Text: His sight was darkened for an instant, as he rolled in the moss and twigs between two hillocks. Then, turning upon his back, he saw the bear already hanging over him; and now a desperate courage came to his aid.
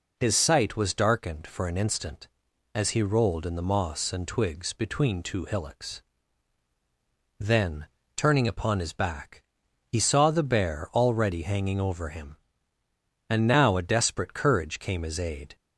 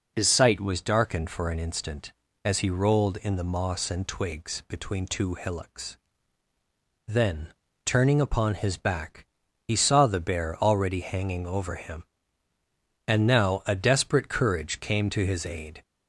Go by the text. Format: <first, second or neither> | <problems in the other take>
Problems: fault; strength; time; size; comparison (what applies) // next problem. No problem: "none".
second | skips "to"; at 15.0 s